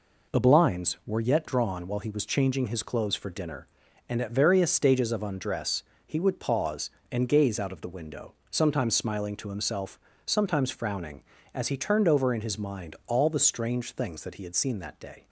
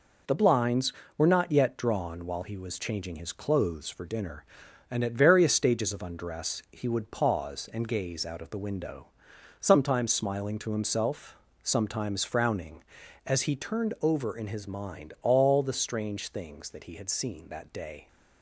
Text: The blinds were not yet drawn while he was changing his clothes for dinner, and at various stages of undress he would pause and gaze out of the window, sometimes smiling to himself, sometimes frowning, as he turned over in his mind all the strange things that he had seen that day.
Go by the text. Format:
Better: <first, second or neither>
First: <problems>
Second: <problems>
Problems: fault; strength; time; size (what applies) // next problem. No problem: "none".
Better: second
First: skips "not"; at 1.2 s // pauses between "undress" and "he"; slight; at 5.8 s; 0.22 s long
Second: none